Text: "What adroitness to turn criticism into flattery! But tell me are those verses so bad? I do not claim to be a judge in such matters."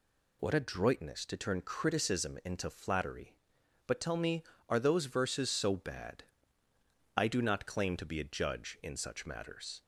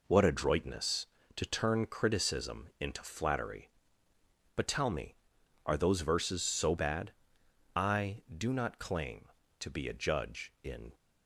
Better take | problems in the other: first | stops before "such matters"; at 10.9 s

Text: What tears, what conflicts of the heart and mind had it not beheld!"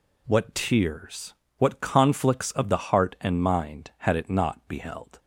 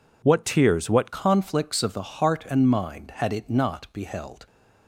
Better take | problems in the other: first | changes voice at "conflicts"; from 1.1 s on; 3.3 s long

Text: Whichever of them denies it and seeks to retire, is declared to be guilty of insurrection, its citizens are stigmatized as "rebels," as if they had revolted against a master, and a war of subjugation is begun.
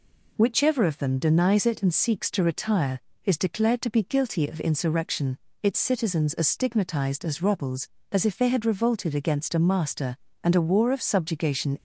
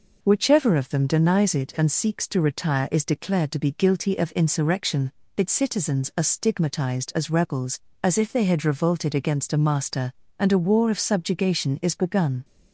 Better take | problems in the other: second | stops before "is begun"; at 11.7 s

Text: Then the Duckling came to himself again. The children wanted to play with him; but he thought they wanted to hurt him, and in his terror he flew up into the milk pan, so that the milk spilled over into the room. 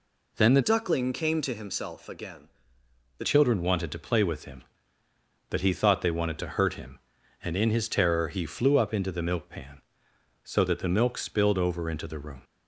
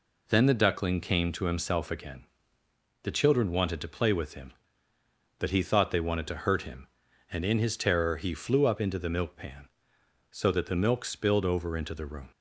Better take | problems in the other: second | changes voice from "Duckling" to "The"; from 0.6 to 3.2 s; 2.6 s long

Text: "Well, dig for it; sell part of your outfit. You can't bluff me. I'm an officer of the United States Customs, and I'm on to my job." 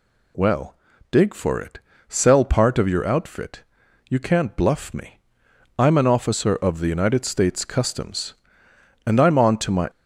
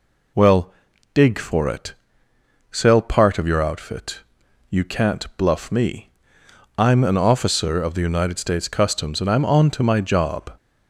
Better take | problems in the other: second | stops before "job"; at 9.8 s

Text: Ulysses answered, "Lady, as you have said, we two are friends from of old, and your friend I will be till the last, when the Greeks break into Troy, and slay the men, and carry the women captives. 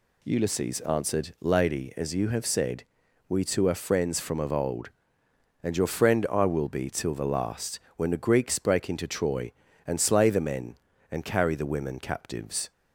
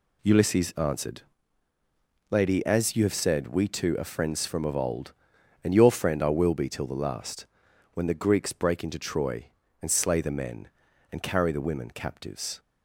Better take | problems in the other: first | gets quieter; strong; throughout; 8 dB

